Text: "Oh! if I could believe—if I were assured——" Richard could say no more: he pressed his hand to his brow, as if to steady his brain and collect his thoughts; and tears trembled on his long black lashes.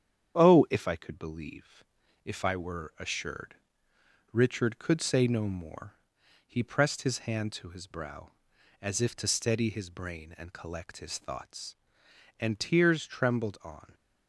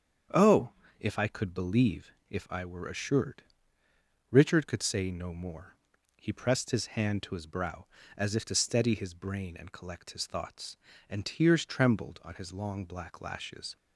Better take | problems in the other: second | starts louder than the rest; strong; until 1.3 s; 8.5 dB; strong in the second // stops before "his long black lashes"; at 13.9 s

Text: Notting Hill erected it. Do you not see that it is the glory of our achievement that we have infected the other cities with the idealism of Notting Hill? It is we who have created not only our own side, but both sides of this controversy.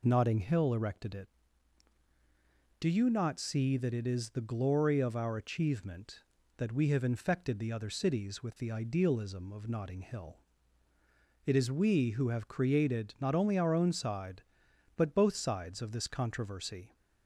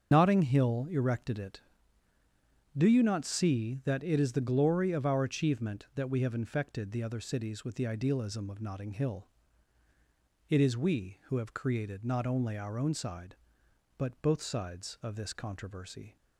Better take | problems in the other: first | loses the start of "Notting"; at 0.1 s; 75 ms // starts louder than the rest; until 1.1 s; 7 dB

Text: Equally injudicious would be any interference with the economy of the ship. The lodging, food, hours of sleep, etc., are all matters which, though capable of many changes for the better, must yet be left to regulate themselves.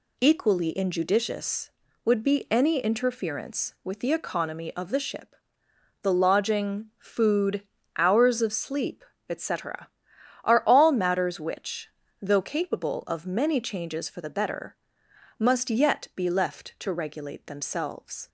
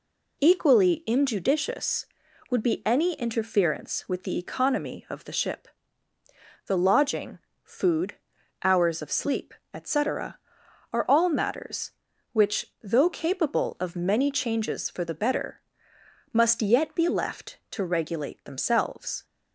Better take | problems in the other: neither | none

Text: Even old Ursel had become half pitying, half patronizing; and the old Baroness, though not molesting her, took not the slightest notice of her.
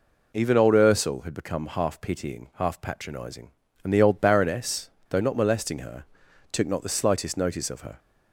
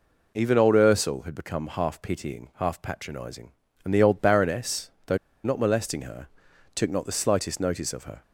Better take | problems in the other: first | pauses between "though" and "not"; slight; at 5.1 s; 0.26 s long

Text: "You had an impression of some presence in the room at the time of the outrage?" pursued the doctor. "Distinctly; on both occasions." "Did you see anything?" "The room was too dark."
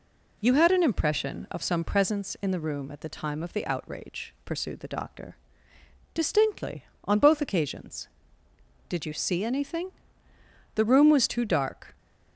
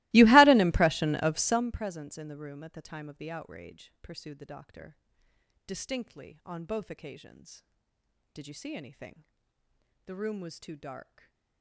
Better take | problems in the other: first | starts louder than the rest; strong; until 1.7 s; 22 dB // stays silent after the last word; slight; from 11.0 s on; 0.6 s long

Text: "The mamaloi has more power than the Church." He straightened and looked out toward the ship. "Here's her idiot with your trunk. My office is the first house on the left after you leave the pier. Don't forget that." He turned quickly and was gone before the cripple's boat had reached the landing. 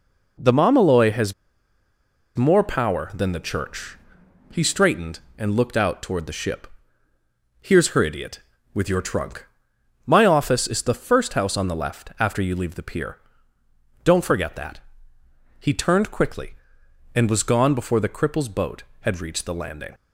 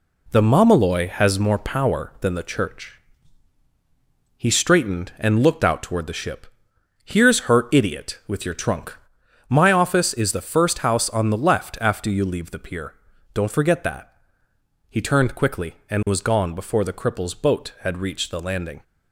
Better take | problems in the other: second | pauses between "has" and "more"; at 1.3 s; 1.0 s long

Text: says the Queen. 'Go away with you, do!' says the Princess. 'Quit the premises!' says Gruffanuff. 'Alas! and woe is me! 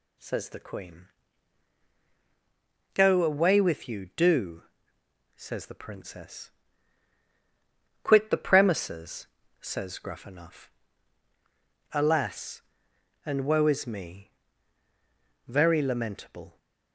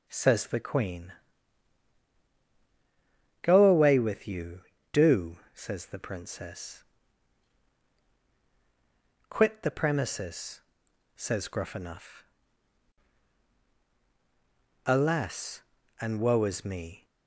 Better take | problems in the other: second | goes on to say "very lamentable"; noticeable; from 15.4 s on; 1.1 s long

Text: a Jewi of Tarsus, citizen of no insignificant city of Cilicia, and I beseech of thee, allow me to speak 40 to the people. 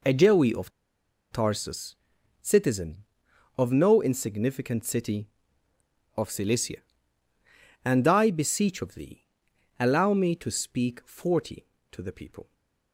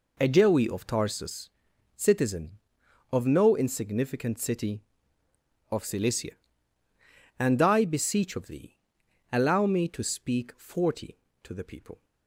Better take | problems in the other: second | pauses between "of" and "Tarsus"; noticeable; at 0.7 s; 0.61 s long // stays silent after the last word; slight; from 12.4 s on; 0.5 s long

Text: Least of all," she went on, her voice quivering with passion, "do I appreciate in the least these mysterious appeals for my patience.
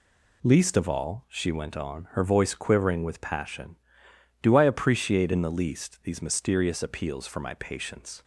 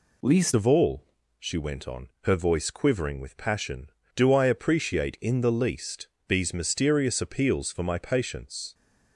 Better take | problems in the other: first | changes voice at "of"; from 0.5 s on; 8.2 s long // pauses between "least" and "these"; slight; at 6.0 s; 0.18 s long

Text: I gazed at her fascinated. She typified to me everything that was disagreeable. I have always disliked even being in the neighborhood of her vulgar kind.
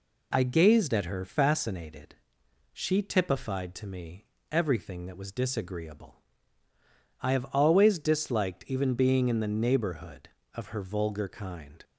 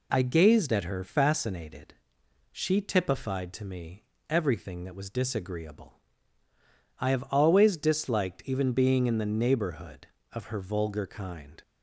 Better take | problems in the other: neither | pauses between "me" and "everything"; slight; the same in both

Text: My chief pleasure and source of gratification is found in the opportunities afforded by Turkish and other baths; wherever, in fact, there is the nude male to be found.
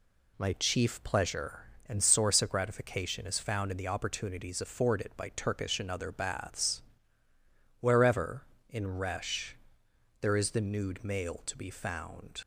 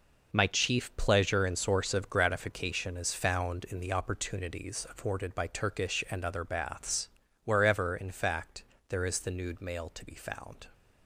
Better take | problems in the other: second | says "resh" for "fact"; at 8.9 s

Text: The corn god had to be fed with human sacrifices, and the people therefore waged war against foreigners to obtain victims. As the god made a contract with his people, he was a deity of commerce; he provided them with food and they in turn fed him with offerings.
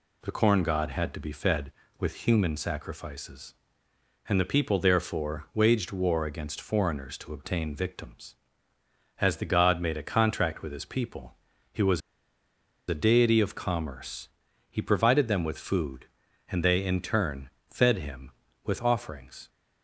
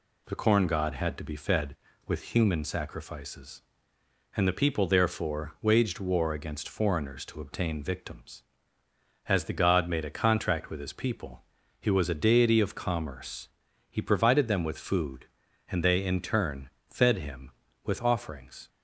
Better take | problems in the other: second | pauses between "was" and "a"; noticeable; at 12.0 s; 0.88 s long // pauses between "turn" and "fed"; slight; at 17.5 s; 0.18 s long; slight in the second

